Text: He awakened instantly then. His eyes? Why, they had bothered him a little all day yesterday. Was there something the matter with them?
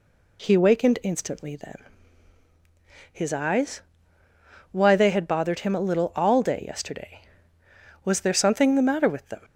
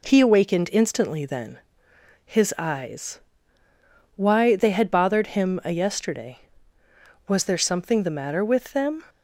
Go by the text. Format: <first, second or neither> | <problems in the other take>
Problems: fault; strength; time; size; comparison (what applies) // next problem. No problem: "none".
first | skips "little all day"; at 5.7 s